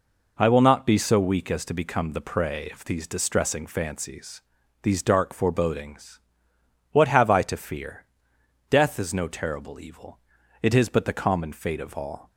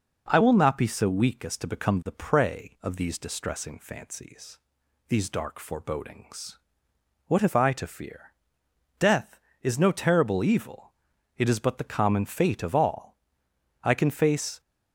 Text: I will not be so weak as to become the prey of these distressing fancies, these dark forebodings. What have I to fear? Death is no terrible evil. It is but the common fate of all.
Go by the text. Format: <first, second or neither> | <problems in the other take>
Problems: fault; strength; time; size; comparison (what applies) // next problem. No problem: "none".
first | goes on to say "I can face"; noticeable; from 13.8 s on; 0.78 s long